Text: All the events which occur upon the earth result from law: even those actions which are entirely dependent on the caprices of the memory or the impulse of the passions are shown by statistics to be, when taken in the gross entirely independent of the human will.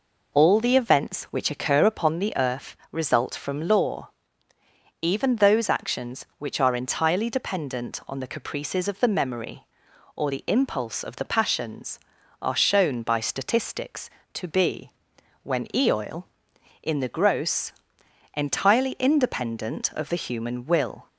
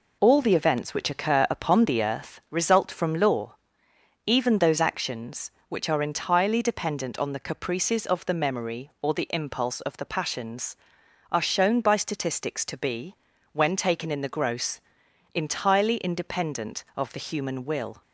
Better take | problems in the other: second | pauses between "earth" and "result"; slight; at 2.7 s; 0.16 s long // says "eoil" for "taken"; at 15.7 s // pauses between "gross" and "entirely"; noticeable; at 17.7 s; 0.60 s long; noticeable in the second

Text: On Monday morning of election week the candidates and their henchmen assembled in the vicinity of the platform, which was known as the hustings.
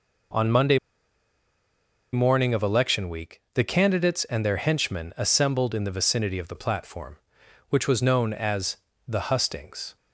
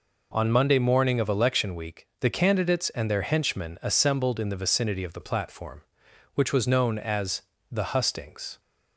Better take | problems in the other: second | pauses between "Monday" and "morning"; strong; at 0.7 s; 1.3 s long // pauses between "as" and "the"; slight; at 8.7 s; 0.32 s long; slight in the second

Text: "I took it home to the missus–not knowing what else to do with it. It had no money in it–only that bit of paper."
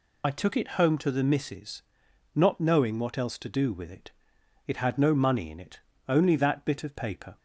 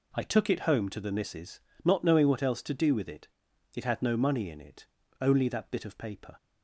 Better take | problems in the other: second | loses the start of "I"; at 0.2 s; 40 ms

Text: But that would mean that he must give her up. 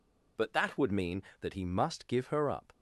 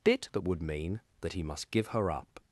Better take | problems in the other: first | says "Bit" for "But"; at 0.0 s

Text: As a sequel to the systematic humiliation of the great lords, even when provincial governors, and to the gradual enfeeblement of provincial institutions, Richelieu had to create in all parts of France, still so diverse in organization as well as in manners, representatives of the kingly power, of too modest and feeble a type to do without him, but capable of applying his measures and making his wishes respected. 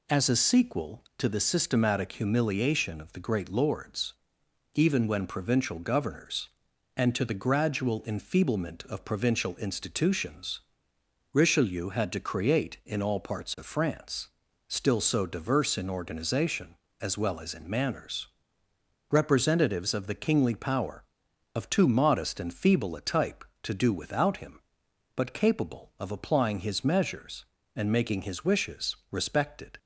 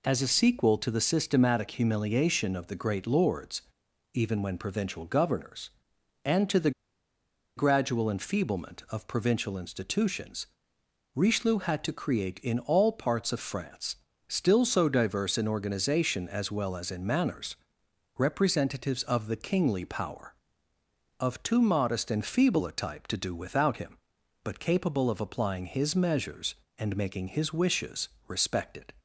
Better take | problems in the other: first | pauses between "the" and "gradual"; noticeable; at 6.7 s; 0.86 s long // pauses between "wishes" and "respected"; slight; at 28.0 s; 0.18 s long

